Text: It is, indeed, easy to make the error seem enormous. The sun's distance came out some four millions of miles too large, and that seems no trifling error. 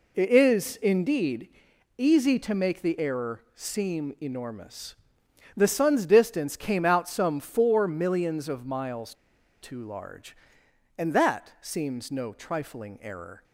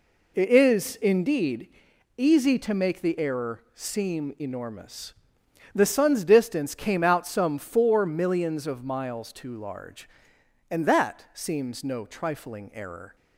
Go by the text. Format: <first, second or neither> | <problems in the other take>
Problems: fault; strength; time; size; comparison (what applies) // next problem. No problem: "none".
second | pauses between "miles" and "too"; noticeable; at 9.1 s; 0.48 s long